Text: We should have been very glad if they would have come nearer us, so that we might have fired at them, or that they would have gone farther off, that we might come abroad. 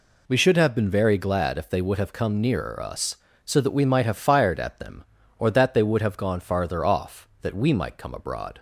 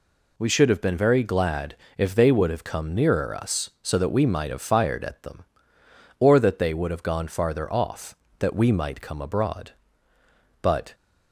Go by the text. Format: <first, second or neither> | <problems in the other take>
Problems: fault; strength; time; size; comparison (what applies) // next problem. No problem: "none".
first | pauses between "glad" and "if"; slight; at 1.7 s; 0.22 s long // goes on to say "But"; slight; from 10.6 s on; 0.32 s long